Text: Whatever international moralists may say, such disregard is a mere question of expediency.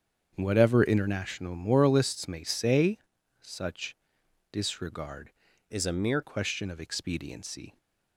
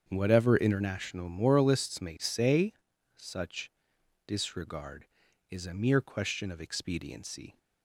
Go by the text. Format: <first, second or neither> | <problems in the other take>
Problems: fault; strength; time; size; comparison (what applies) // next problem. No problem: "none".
second | starts louder than the rest; strong; until 1.3 s; 7.5 dB; strong in the second // pauses between "such" and "disregard"; noticeable; at 3.9 s; 0.56 s long; noticeable in the second // changes voice from "is" to "mere"; from 5.7 to 6.2 s; 0.5 s long